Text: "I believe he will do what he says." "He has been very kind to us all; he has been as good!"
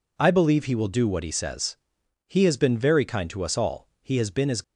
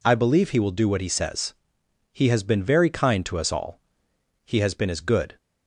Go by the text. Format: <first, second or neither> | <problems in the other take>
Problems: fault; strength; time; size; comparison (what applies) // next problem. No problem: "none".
second | stops before "good"; at 4.6 s